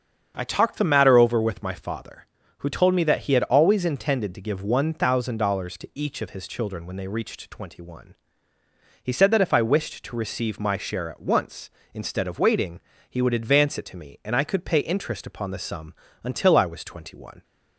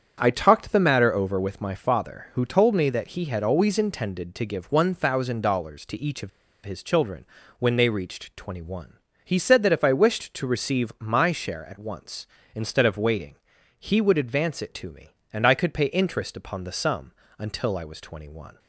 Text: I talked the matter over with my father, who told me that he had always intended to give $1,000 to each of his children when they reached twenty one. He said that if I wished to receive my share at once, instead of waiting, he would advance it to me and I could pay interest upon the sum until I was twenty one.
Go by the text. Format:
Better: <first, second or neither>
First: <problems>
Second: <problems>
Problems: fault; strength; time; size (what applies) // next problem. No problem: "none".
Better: first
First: starts louder than the rest; strong; until 1.3 s; 7.5 dB // pauses between "sum" and "until"; slight; at 15.9 s; 0.30 s long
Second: starts louder than the rest; strong; until 1.2 s; 8 dB // pauses between "of" and "his"; at 6.2 s; 0.36 s long // pauses between "children" and "when"; slight; at 7.2 s; 0.34 s long // pauses between "sum" and "until"; slight; at 17.1 s; 0.26 s long